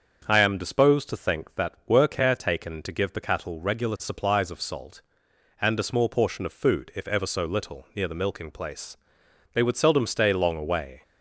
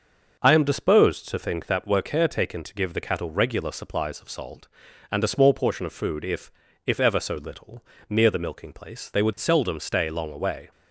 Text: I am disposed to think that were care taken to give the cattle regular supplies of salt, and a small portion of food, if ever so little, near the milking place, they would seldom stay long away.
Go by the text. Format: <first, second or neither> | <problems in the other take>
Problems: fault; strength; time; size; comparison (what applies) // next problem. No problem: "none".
first | starts louder than the rest; until 1.4 s; 6.5 dB; also in the first // says "if" twice; at 6.8 s